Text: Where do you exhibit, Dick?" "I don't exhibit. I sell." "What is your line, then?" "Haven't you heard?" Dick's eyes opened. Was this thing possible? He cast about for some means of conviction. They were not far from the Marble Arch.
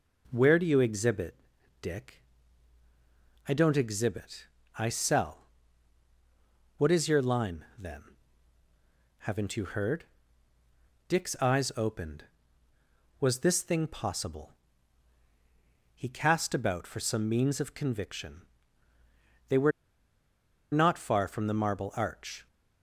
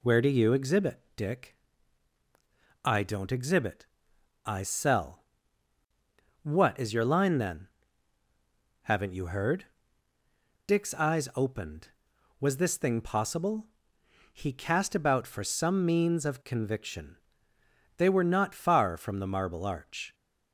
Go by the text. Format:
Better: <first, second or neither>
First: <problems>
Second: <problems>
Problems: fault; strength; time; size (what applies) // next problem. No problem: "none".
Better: second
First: pauses between "were" and "not"; at 19.7 s; 1.0 s long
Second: none